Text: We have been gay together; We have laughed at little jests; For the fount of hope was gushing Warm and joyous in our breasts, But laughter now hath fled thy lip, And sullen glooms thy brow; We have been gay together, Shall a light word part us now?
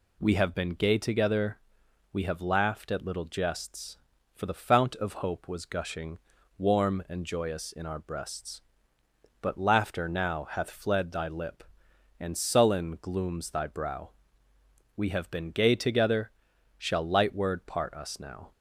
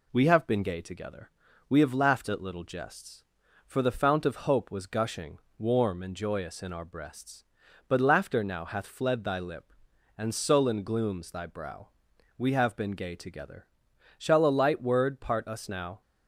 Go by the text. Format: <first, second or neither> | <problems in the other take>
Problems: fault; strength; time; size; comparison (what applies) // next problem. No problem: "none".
second | pauses between "gushing" and "Warm"; at 6.1 s; 0.38 s long; slight in the second // skips "a"; at 17.0 s